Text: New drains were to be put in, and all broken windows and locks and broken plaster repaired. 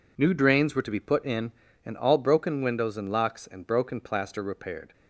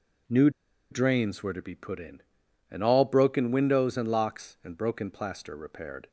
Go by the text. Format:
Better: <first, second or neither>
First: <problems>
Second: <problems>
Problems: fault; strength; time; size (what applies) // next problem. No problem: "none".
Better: first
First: none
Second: pauses between "New" and "drains"; at 0.4 s; 0.41 s long